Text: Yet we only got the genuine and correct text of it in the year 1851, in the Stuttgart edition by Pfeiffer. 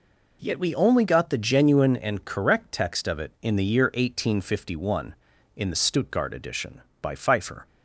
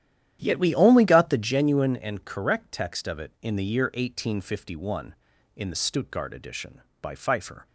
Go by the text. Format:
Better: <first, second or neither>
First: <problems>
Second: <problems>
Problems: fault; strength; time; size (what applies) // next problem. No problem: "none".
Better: first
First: none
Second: starts louder than the rest; strong; until 1.5 s; 11 dB